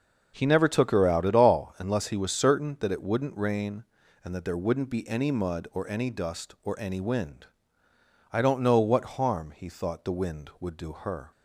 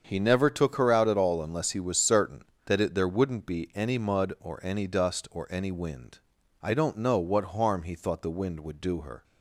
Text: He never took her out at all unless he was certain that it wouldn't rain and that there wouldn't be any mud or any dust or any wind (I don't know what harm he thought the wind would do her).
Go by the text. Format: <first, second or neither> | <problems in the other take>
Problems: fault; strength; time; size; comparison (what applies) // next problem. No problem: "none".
first | starts louder than the rest; until 1.0 s; 7 dB; noticeable in the first // skips "wouldn't rain and that"; at 2.9 s